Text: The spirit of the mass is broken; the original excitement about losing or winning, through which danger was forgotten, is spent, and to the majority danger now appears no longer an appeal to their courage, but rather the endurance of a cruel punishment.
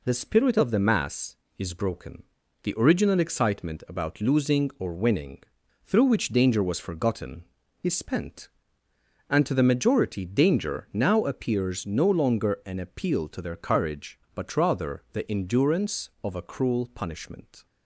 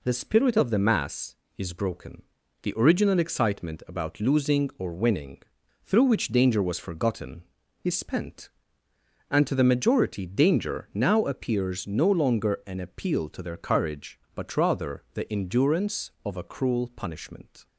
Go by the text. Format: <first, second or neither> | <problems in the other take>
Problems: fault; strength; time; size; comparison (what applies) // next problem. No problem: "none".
neither | none